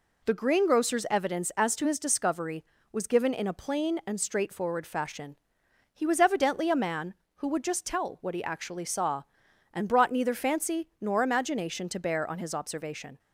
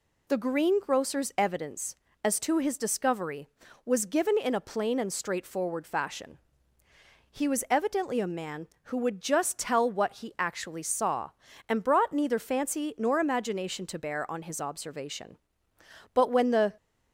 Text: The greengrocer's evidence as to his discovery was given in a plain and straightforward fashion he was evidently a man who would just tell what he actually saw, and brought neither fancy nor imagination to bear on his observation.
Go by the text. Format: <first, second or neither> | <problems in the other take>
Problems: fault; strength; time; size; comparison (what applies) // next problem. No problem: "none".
first | pauses between "fashion" and "he"; noticeable; at 6.3 s; 0.92 s long; noticeable in the first // goes on to say "But when the"; noticeable; from 16.1 s on; 0.62 s long